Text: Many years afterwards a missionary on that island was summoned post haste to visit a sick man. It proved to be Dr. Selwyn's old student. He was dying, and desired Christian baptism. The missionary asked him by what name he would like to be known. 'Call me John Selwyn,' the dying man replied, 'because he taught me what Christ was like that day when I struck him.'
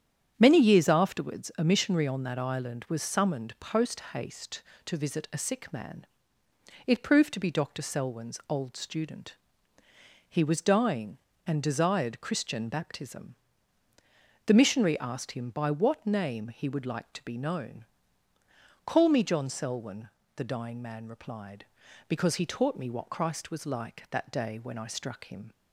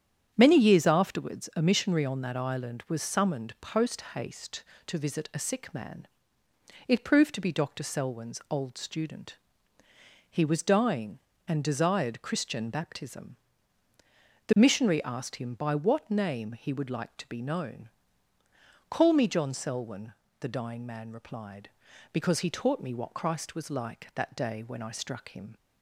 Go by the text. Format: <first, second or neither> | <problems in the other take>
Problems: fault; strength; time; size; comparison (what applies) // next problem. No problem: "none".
neither | starts louder than the rest; strong; the same in both